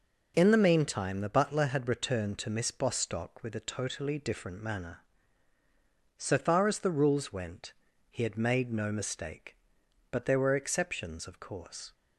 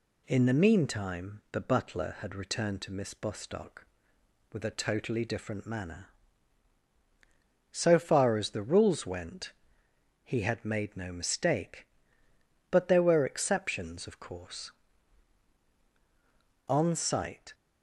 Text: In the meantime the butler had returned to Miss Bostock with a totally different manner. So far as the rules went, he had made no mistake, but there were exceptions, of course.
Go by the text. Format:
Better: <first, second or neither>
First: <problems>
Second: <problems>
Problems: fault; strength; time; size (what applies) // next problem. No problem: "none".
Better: first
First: none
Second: goes on to say "On sight"; noticeable; from 16.6 s on; 0.84 s long